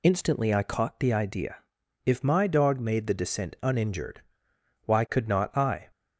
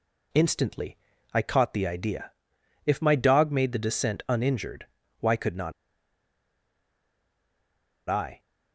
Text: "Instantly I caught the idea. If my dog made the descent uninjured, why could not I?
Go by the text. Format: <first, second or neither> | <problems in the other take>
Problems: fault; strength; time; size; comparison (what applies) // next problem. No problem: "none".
first | pauses between "Instantly" and "I"; slight; at 0.9 s; 0.36 s long // pauses between "not" and "I"; strong; at 5.7 s; 2.3 s long